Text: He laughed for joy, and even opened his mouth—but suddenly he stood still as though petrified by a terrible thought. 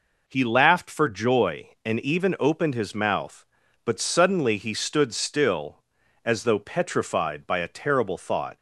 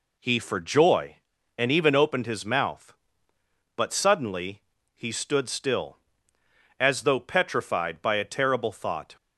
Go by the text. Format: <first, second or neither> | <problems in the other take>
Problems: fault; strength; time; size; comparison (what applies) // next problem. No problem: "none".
first | skips "laughed"; at 0.3 s // pauses between "suddenly" and "he"; slight; at 4.6 s; 0.34 s long